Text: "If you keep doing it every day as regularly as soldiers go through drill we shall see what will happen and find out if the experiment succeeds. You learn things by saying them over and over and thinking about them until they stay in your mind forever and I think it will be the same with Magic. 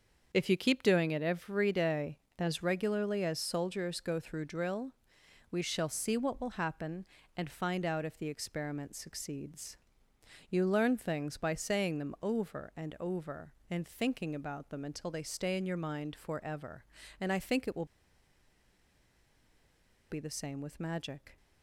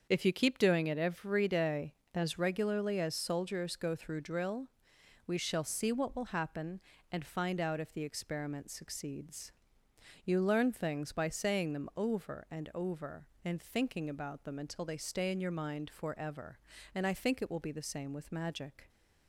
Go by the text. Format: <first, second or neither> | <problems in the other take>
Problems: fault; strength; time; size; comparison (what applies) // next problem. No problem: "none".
second | starts louder than the rest; until 1.3 s; 6.5 dB; also in the second // pauses between "drill" and "we"; noticeable; at 4.9 s; 0.58 s long; noticeable in the second // pauses between "will" and "be"; strong; at 17.8 s; 2.2 s long